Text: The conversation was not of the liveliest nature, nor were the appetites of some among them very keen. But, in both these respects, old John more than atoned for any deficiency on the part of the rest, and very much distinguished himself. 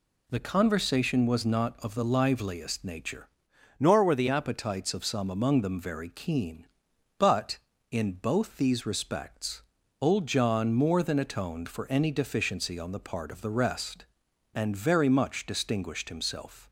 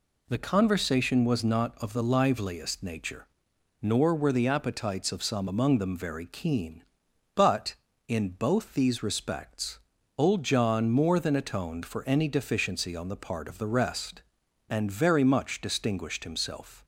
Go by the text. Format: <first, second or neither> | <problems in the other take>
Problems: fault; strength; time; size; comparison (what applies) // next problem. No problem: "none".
second | changes voice from "nor" to "the"; from 3.7 to 4.2 s; 0.5 s long